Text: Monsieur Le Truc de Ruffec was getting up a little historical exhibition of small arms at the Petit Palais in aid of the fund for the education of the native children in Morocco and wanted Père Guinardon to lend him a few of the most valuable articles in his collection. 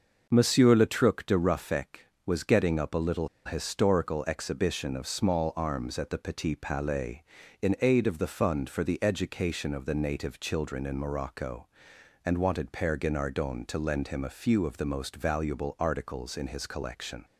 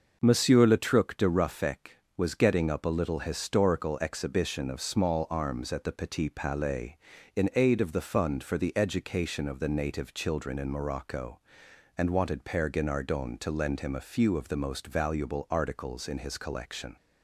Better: second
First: pauses between "little" and "historical"; slight; at 3.2 s; 0.17 s long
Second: none

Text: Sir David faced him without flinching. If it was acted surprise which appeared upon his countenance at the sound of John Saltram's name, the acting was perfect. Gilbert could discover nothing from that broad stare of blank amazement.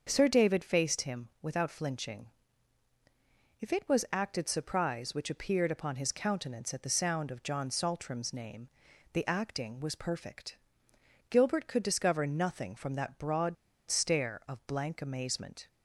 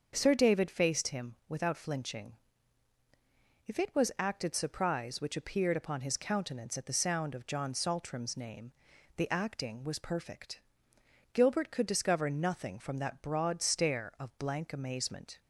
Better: second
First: starts louder than the rest; until 1.0 s; 6.5 dB // pauses between "broad" and "stare"; slight; at 13.5 s; 0.34 s long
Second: starts louder than the rest; until 1.1 s; 6.5 dB

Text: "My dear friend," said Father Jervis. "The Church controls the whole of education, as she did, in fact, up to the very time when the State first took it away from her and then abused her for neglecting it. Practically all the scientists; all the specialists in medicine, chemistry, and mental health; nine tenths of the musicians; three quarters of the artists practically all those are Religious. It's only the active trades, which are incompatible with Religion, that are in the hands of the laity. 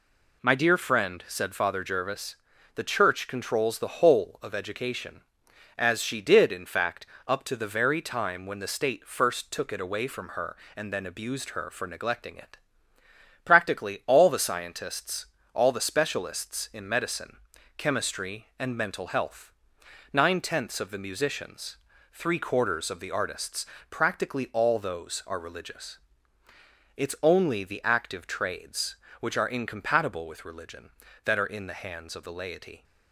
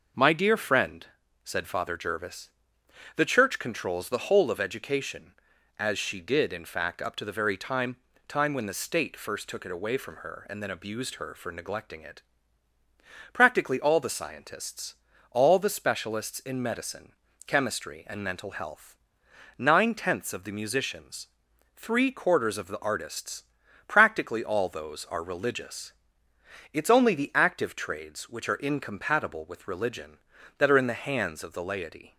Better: first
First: pauses between "artists" and "practically"; slight; at 23.6 s; 0.24 s long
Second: says "time" twice; at 8.2 s // pauses between "artists" and "practically"; noticeable; at 23.4 s; 0.46 s long

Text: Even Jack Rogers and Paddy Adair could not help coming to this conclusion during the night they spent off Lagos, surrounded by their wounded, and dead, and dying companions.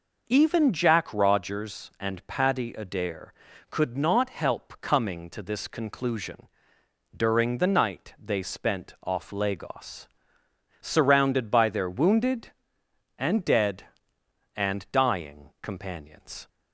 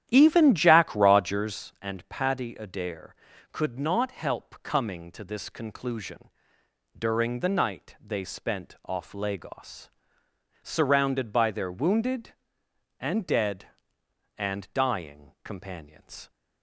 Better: first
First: pauses between "conclusion" and "during"; noticeable; at 6.4 s; 0.66 s long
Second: starts louder than the rest; strong; until 1.7 s; 11 dB // pauses between "conclusion" and "during"; noticeable; at 6.2 s; 0.66 s long

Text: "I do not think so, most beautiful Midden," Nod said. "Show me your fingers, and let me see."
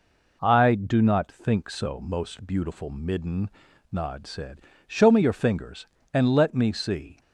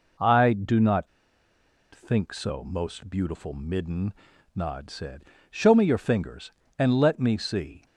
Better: first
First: none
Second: pauses between "not" and "think"; noticeable; at 1.0 s; 0.87 s long

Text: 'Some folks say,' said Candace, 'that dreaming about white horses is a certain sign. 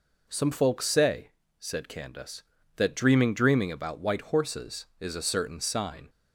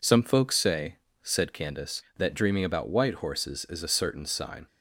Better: second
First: says "dreaming" twice; at 3.3 s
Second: none

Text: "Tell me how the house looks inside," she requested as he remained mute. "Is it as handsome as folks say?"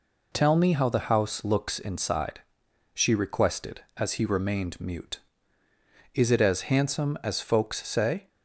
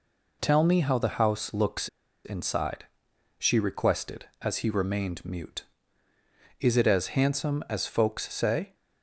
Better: first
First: none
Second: pauses between "looks" and "inside"; at 1.8 s; 0.38 s long

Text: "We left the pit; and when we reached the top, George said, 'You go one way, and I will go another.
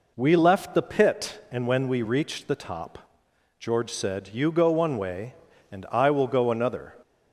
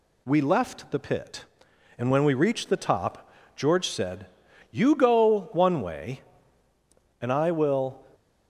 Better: first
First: none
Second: stops before "go another"; at 8.1 s

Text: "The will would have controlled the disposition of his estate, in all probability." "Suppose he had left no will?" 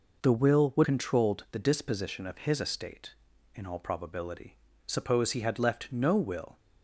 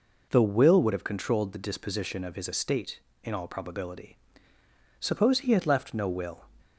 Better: second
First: skips "have"; at 0.8 s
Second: none

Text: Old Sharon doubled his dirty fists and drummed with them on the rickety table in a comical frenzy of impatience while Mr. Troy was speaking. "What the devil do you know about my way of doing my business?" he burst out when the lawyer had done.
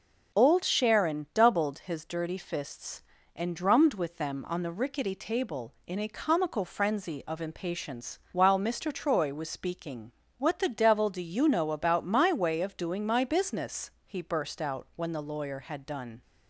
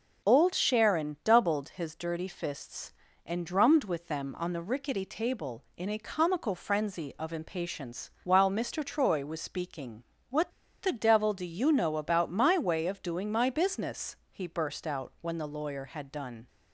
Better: first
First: starts louder than the rest; until 1.4 s; 6.5 dB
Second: starts louder than the rest; until 1.3 s; 6 dB // pauses between "What" and "the"; slight; at 10.5 s; 0.32 s long

